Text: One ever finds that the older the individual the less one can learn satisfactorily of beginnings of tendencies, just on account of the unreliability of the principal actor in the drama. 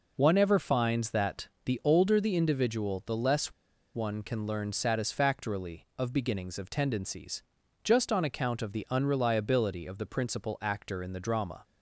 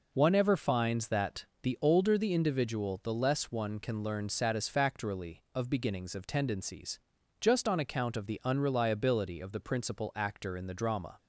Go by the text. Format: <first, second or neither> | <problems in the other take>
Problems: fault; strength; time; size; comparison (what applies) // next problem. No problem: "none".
second | pauses between "that" and "the"; slight; at 1.4 s; 0.18 s long; slight in the second // pauses between "less" and "one"; at 3.5 s; 0.41 s long